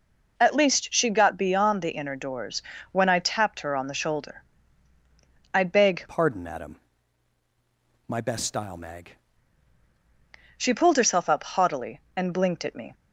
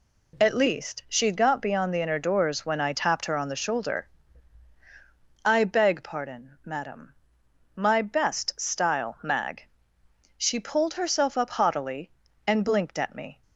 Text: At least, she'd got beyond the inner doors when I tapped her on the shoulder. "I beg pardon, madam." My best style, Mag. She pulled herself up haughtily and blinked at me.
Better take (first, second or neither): second